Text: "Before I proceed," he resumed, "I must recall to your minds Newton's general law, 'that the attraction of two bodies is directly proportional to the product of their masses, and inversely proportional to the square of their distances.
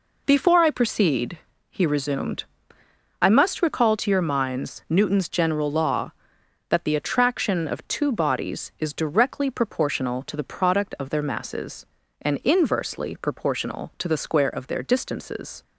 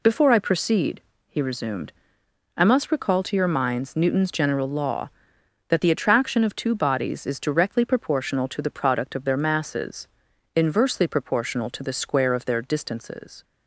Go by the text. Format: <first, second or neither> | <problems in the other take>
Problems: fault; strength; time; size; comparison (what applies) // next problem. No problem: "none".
first | skips "and"; at 10.3 s